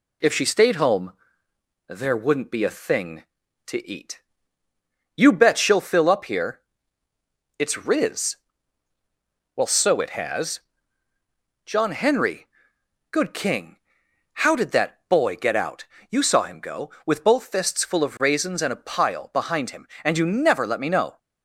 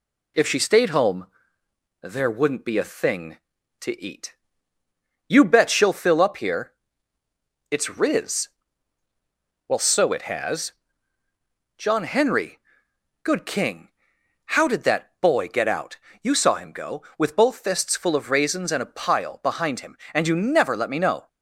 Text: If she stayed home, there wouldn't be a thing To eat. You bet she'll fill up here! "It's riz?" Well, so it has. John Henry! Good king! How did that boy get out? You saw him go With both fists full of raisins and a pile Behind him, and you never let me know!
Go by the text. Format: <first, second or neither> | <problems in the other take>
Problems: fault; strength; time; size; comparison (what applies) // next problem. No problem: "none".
neither | none